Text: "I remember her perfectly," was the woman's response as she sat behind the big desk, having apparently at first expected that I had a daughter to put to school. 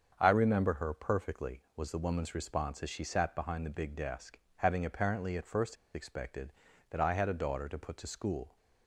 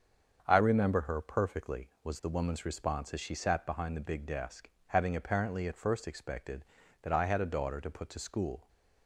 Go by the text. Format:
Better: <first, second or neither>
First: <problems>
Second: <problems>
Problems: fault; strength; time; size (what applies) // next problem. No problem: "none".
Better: second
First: starts louder than the rest; until 1.2 s; 7 dB // pauses between "first" and "expected"; slight; at 5.7 s; 0.19 s long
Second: starts louder than the rest; until 1.4 s; 7 dB